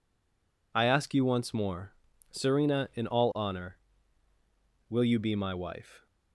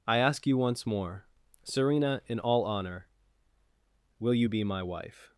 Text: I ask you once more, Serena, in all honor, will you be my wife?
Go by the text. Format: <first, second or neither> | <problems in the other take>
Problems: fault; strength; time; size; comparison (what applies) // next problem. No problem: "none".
second | stays silent before the first word; slight; until 0.7 s; 0.7 s long